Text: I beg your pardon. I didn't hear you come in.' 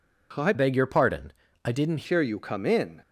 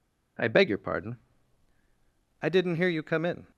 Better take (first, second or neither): second